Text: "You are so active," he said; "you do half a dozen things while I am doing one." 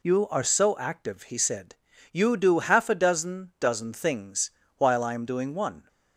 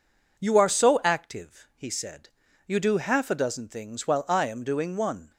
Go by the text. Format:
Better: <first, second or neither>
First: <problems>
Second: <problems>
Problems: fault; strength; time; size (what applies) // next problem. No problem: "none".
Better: second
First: says "dozen" twice; at 3.5 s // pauses between "things" and "while"; slight; at 4.5 s; 0.24 s long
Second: none